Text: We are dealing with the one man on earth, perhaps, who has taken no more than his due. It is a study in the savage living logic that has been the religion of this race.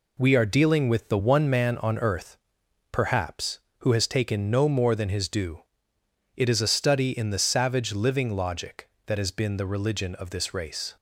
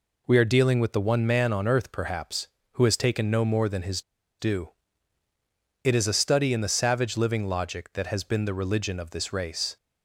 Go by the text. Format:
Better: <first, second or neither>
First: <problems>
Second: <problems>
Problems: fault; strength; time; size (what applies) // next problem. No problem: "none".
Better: first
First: none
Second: pauses between "his" and "due"; at 4.0 s; 0.39 s long